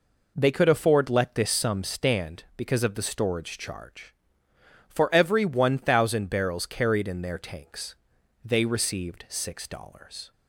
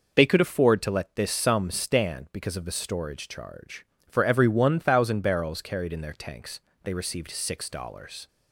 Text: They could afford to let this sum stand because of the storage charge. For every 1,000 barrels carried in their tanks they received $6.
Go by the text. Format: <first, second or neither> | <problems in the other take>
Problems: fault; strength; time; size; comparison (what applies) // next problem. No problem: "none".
second | skips "to"; at 1.0 s // pauses between "tanks" and "they"; noticeable; at 7.9 s; 0.50 s long; slight in the second